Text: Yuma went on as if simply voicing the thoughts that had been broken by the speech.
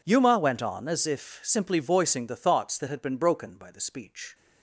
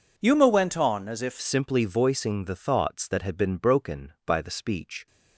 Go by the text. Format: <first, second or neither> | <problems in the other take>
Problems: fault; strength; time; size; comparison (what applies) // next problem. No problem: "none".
first | changes voice at "simply"; from 1.4 s on; 3.6 s long